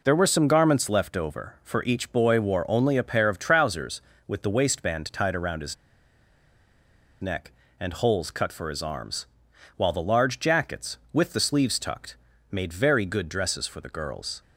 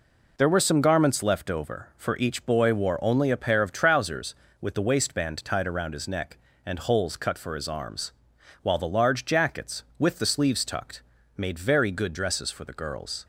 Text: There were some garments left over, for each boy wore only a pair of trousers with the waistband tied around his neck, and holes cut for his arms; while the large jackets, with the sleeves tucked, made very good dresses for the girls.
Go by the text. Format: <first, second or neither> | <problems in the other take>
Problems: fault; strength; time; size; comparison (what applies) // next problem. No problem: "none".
second | pauses between "his" and "neck"; strong; at 5.7 s; 1.4 s long